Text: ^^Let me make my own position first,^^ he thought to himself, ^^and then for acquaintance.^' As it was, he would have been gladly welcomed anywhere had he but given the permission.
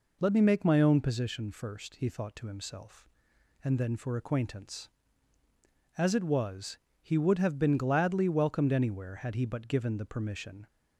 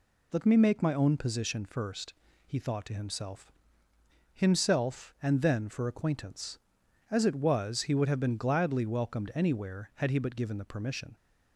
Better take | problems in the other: first | says "himself" twice; at 4.3 s

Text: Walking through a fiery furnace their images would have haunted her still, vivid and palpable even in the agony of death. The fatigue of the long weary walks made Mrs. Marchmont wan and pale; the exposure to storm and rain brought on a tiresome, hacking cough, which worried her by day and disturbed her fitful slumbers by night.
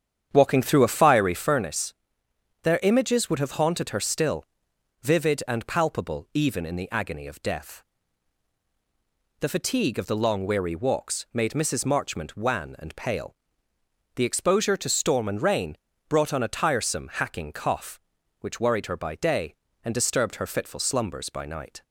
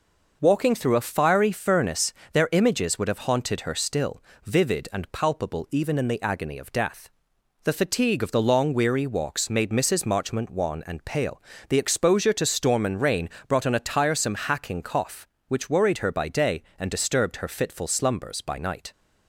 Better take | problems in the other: second | starts louder than the rest; strong; until 1.6 s; 8.5 dB // pauses between "furnace" and "their"; noticeable; at 1.9 s; 0.70 s long; slight in the second // pauses between "rain" and "brought"; slight; at 15.7 s; 0.32 s long; slight in the second

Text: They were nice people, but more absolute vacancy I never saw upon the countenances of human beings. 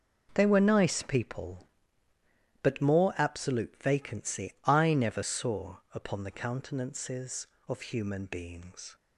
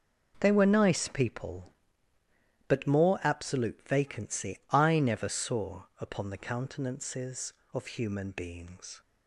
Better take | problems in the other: neither | none

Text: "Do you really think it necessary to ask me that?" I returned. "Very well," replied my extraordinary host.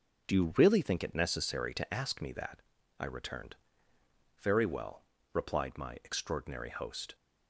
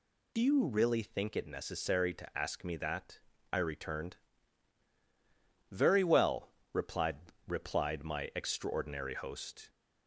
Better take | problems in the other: first | says "replied" twice; at 7.4 s

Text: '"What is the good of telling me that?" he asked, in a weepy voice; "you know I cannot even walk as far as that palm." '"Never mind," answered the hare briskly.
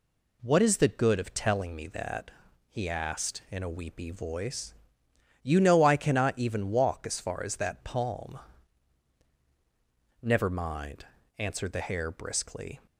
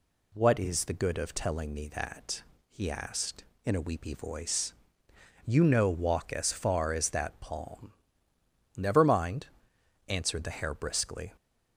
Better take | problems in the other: first | skips "I cannot even"; at 5.8 s

